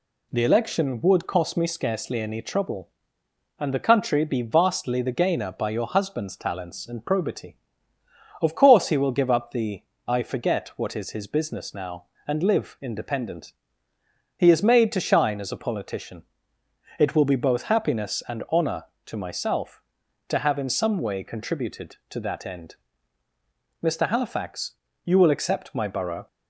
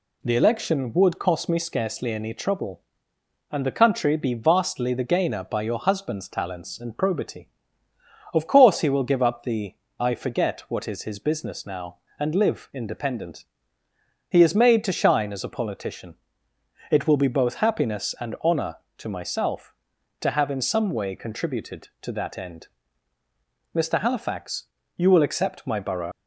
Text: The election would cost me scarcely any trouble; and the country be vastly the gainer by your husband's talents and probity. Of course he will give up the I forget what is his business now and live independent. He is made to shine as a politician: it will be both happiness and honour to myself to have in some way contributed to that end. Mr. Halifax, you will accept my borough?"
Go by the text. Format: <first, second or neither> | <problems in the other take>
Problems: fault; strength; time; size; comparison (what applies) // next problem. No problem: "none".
first | pauses between "the" and "I"; slight; at 9.7 s; 0.24 s long; slight in the first // leaves "borough" unfinished; at 26.1 s; 70 ms